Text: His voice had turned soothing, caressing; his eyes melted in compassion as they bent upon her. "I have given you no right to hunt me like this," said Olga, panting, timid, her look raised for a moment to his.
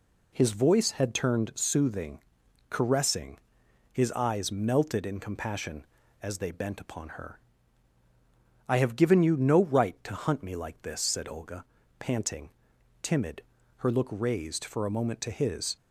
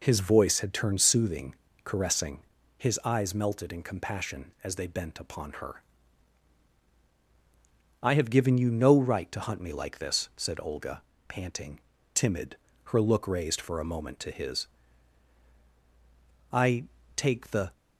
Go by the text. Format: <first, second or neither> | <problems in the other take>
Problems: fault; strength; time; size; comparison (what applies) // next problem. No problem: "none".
first | goes on to say "I take the"; noticeable; from 16.5 s on; 1.2 s long